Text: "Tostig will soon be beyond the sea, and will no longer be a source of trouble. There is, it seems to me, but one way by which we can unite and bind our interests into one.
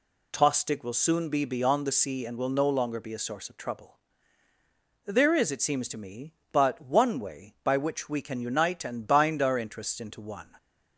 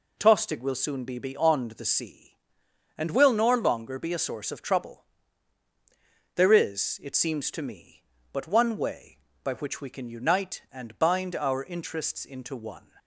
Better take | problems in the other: first | says "nor" for "no"; at 3.3 s

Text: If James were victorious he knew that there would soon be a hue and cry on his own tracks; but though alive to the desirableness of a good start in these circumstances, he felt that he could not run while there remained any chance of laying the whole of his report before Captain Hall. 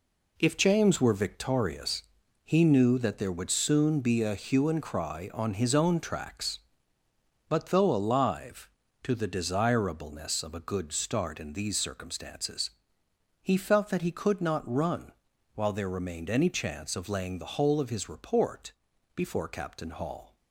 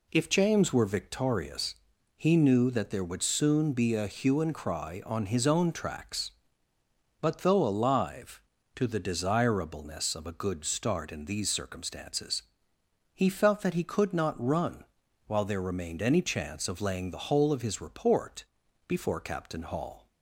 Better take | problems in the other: second | gets quieter; strong; throughout; 8.5 dB // pauses between "victorious" and "he"; noticeable; at 2.0 s; 0.46 s long; noticeable in the second // pauses between "run" and "while"; at 15.1 s; 0.44 s long; also in the second // pauses between "report" and "before"; at 18.7 s; 0.42 s long; also in the second

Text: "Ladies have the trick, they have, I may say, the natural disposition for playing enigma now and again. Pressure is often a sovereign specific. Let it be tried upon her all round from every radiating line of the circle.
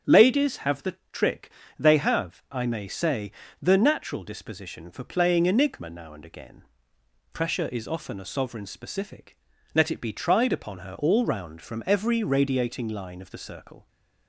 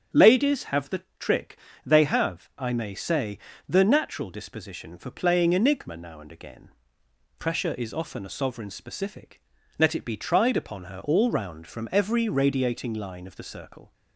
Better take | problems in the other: neither | starts louder than the rest; strong; the same in both // pauses between "the" and "trick"; slight; the same in both

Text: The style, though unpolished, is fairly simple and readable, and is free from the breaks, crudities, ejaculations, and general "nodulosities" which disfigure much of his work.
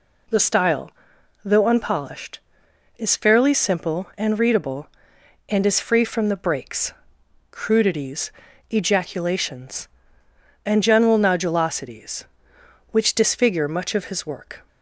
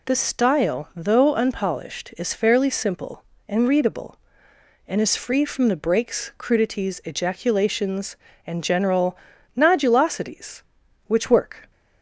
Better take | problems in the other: first | pauses between "general" and "nodulosities"; at 9.1 s; 0.40 s long // skips "disfigure much of his"; at 11.3 s

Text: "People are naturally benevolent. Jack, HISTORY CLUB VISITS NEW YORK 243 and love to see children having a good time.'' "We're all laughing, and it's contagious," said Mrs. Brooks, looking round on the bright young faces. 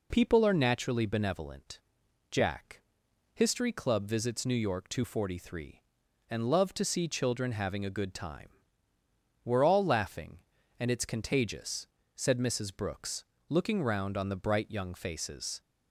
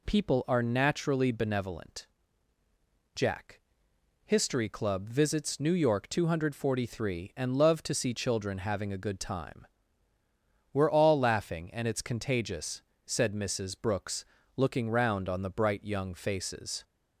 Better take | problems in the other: neither | none

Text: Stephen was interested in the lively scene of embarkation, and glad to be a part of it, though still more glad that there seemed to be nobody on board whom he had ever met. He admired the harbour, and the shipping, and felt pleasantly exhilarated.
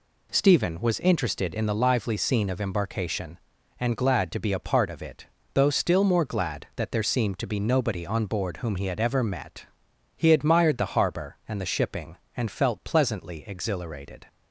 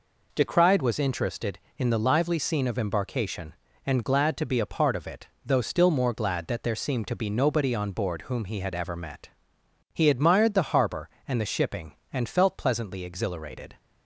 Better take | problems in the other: first | says "Decried" for "Stephen"; at 0.3 s

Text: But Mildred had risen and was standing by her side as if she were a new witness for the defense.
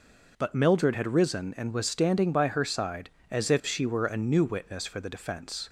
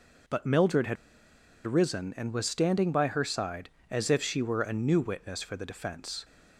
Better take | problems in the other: first | pauses between "had" and "risen"; noticeable; at 0.9 s; 0.70 s long

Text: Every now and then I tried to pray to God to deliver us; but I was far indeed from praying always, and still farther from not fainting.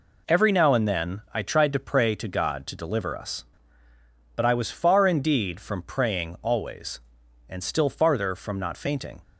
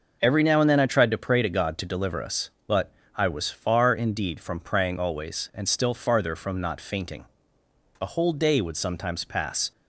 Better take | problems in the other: first | pauses between "but" and "I"; slight; at 2.9 s; 0.24 s long // goes on to say "A whole day would sometimes pass"; strong; from 8.0 s on; 1.7 s long

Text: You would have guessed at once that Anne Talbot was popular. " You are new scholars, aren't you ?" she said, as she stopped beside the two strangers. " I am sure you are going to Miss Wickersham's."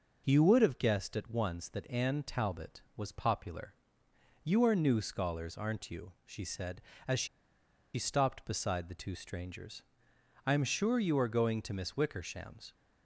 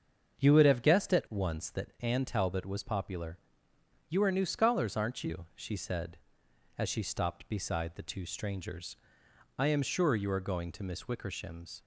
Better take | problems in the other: second | starts louder than the rest; until 1.2 s; 6 dB; strong in the second // pauses between "she" and "stopped"; noticeable; at 7.2 s; 0.69 s long

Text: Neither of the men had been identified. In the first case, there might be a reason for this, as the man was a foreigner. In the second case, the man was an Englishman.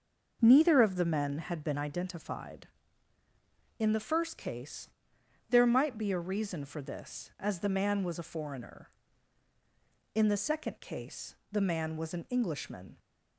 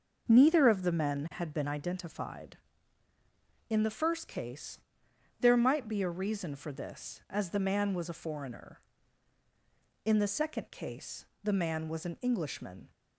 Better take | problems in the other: neither | starts louder than the rest; the same in both

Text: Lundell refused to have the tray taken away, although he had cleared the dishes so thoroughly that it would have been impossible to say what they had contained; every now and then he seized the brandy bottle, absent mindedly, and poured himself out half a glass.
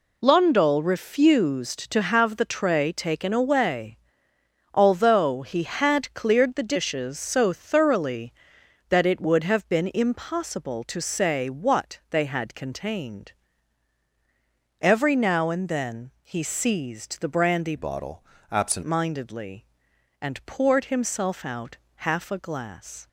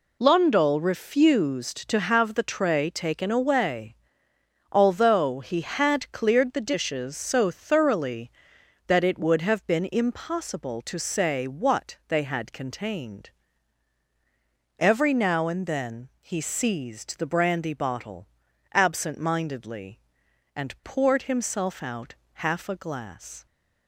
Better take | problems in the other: second | changes voice from "bottle" to "absent"; from 17.7 to 18.8 s; 1.1 s long // pauses between "out" and "half"; slight; at 21.7 s; 0.18 s long; slight in the second

